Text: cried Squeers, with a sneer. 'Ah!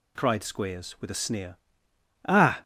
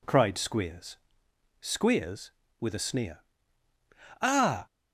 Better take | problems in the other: first | says "Squeers" twice; at 1.6 s

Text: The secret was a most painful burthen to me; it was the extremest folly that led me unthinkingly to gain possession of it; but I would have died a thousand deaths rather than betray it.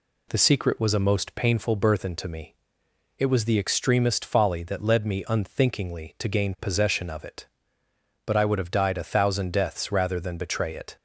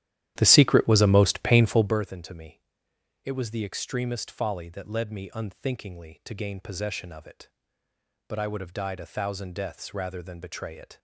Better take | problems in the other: first | starts louder than the rest; strong; until 2.0 s; 12.5 dB

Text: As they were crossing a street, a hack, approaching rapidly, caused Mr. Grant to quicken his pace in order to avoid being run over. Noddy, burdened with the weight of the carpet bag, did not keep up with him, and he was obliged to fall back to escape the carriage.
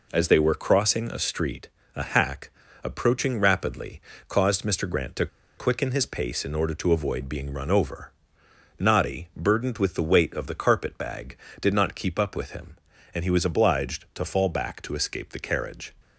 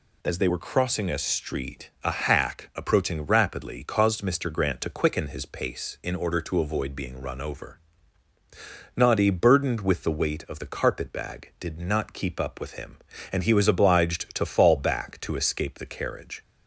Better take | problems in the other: second | pauses between "to" and "quicken"; slight; at 5.2 s; 0.32 s long

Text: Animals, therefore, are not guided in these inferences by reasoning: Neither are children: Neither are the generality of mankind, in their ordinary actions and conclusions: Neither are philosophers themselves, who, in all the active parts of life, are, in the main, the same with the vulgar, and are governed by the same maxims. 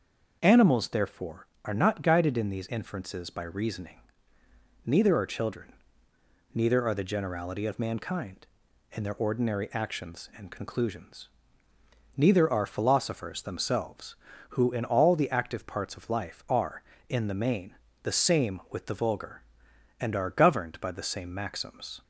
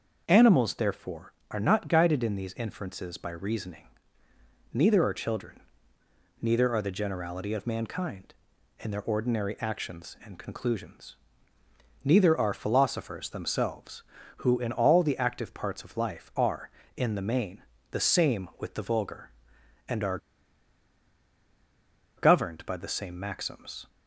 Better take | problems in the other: first | starts louder than the rest; noticeable; until 1.2 s; 6 dB; noticeable in the first // pauses between "are" and "governed"; strong; at 20.1 s; 2.0 s long

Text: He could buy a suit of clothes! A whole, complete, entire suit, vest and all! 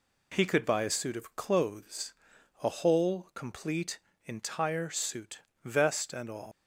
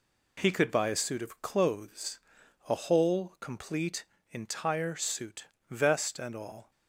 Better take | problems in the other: second | leaves "all" unfinished; at 6.5 s; 130 ms

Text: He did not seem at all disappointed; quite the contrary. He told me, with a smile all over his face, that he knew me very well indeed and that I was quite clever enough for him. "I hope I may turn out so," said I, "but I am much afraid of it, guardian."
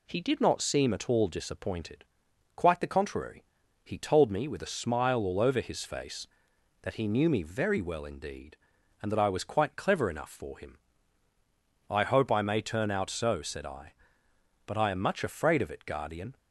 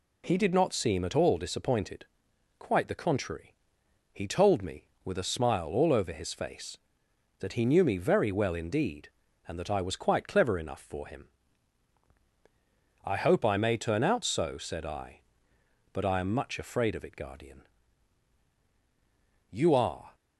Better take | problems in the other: first | goes on to say "You are"; noticeable; from 19.5 s on; 0.64 s long

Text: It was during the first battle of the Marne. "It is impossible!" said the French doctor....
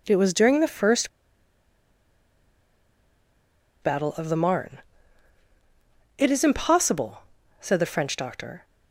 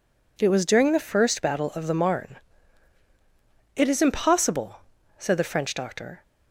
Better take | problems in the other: second | pauses between "first" and "battle"; strong; at 1.0 s; 2.7 s long

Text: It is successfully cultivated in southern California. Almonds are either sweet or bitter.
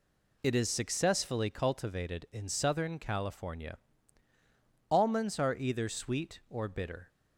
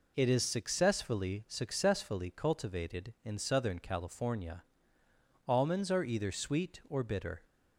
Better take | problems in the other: first | says "successfully" twice; at 1.4 s

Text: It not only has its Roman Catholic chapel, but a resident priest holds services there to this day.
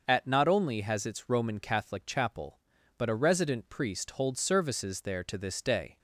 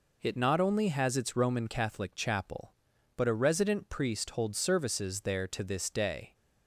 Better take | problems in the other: second | starts louder than the rest; noticeable; until 1.0 s; 6 dB // says "At" for "It"; at 0.0 s

